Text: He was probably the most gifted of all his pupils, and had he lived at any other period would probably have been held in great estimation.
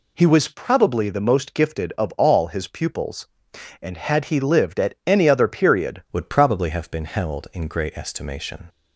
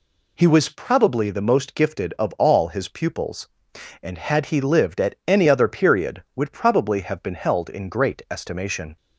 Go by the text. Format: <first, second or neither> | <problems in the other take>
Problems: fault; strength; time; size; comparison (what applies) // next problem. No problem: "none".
second | changes voice at "would"; from 6.1 s on; 2.5 s long